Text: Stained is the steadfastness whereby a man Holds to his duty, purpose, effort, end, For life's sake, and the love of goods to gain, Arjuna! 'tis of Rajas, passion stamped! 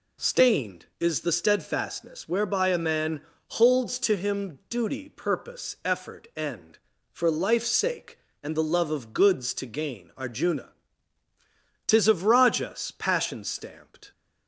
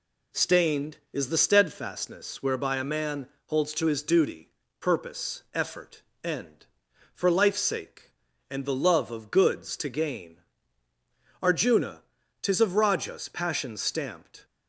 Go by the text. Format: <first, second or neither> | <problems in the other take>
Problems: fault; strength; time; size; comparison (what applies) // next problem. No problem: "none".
second | pauses between "man" and "Holds"; slight; at 3.2 s; 0.32 s long; slight in the second // says "him" for "his"; at 4.1 s